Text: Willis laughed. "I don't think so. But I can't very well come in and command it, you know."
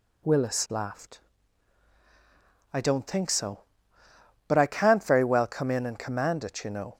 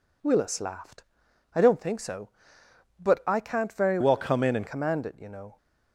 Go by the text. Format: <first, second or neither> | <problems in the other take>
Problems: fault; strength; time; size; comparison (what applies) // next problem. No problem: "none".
first | changes voice from "well" to "and"; from 4.0 to 4.6 s; 0.6 s long